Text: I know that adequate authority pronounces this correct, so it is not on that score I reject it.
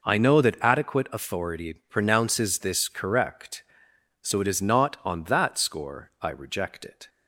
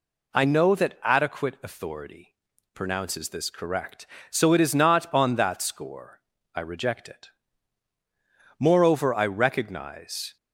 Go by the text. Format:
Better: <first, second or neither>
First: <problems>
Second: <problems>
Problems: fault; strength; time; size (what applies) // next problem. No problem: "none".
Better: first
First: pauses between "authority" and "pronounces"; slight; at 1.7 s; 0.16 s long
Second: pauses between "authority" and "pronounces"; at 2.3 s; 0.38 s long // pauses between "score" and "I"; slight; at 6.1 s; 0.34 s long // goes on to say "Moreover I recognize"; strong; from 8.5 s on; 1.7 s long